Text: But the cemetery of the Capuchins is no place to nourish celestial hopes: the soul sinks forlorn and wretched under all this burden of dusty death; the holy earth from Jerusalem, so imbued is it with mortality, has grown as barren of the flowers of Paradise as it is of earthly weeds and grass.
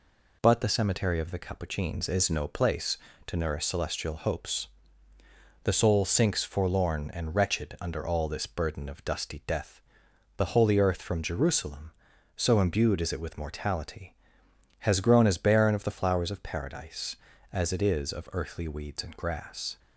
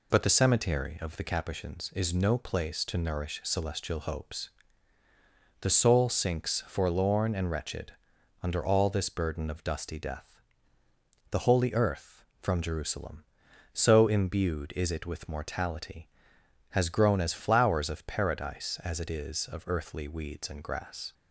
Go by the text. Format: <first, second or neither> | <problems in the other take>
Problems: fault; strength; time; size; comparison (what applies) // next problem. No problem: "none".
first | pauses between "wretched" and "under"; noticeable; at 7.9 s; 0.50 s long // skips "barren of the"; at 17.3 s